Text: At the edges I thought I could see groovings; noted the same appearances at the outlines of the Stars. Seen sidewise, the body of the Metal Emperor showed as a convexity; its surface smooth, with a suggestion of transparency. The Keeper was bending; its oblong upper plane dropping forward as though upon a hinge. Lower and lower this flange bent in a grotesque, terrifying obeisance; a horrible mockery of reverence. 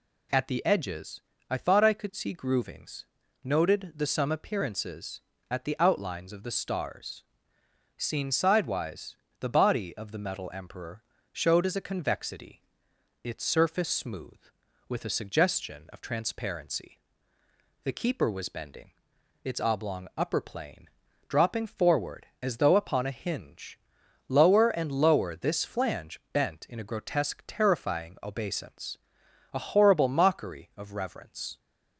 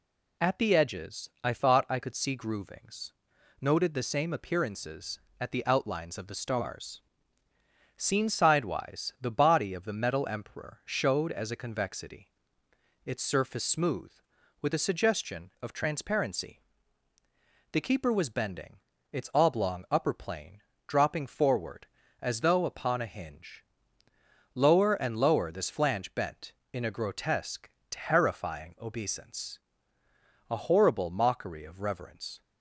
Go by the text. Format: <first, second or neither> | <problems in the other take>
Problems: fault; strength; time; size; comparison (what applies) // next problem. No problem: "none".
second | pauses between "edges" and "I"; slight; at 1.1 s; 0.30 s long // says "some" for "same"; at 4.0 s // pauses between "Emperor" and "showed"; slight; at 11.0 s; 0.30 s long // pauses between "plane" and "dropping"; at 20.8 s; 0.40 s long; slight in the second